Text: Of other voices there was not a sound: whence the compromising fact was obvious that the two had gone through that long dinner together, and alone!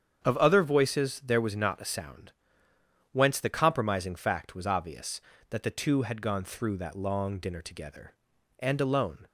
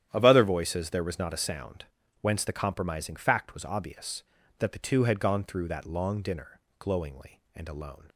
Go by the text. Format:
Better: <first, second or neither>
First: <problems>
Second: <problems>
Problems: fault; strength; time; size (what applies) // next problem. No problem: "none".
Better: first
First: starts louder than the rest; strong; until 1.3 s; 8 dB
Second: starts louder than the rest; strong; until 1.1 s; 10.5 dB // says "glowingly" for "together"; at 6.7 s